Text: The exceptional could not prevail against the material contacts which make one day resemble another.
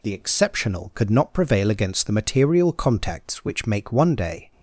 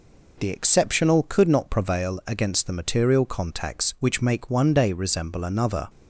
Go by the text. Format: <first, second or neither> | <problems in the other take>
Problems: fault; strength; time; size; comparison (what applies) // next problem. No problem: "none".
second | stops before "resemble another"; at 4.5 s